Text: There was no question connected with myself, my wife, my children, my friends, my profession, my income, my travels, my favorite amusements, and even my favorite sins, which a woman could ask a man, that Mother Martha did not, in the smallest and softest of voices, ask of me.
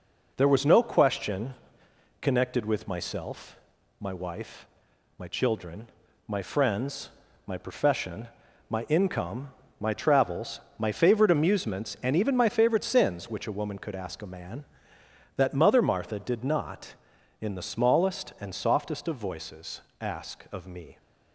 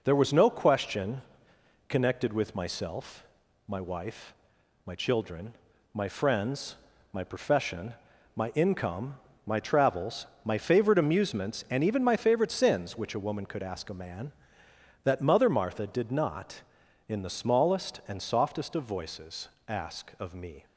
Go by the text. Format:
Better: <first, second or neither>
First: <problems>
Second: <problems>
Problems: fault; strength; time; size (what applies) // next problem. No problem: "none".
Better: neither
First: pauses between "question" and "connected"; noticeable; at 1.5 s; 0.70 s long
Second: pauses between "question" and "connected"; noticeable; at 1.1 s; 0.70 s long